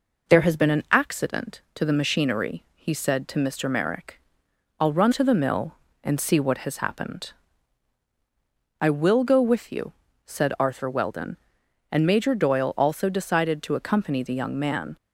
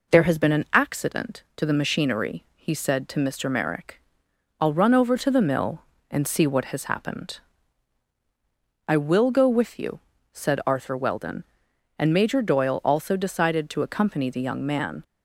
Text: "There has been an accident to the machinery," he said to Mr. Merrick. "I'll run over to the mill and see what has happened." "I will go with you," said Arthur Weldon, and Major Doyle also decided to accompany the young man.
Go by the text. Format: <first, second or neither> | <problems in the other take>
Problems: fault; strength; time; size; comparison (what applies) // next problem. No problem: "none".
second | skips "over"; at 5.1 s